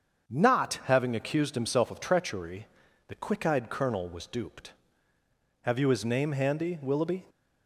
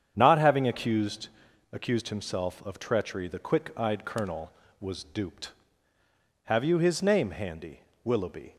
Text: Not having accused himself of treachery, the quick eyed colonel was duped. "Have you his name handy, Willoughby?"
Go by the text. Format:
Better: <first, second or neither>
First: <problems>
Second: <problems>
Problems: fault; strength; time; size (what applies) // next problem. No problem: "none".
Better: first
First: starts louder than the rest; until 1.3 s; 7 dB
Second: starts louder than the rest; strong; until 1.1 s; 8.5 dB // says "accused" twice; at 1.7 s